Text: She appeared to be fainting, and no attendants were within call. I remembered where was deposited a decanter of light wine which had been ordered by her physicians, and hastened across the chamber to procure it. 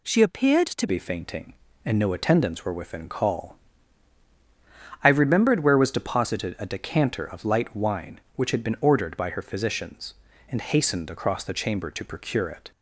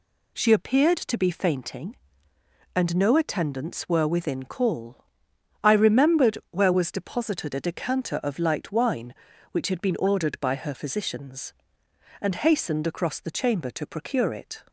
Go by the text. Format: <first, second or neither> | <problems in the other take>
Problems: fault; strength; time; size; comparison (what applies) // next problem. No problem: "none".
second | changes voice at "be"; from 0.8 s on; 11.9 s long